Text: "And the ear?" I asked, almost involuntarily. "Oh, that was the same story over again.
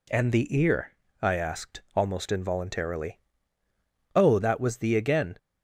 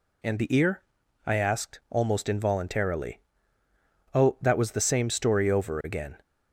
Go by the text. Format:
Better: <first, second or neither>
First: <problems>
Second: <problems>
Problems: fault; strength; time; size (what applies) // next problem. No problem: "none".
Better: second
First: skips "same story over"; at 4.9 s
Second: none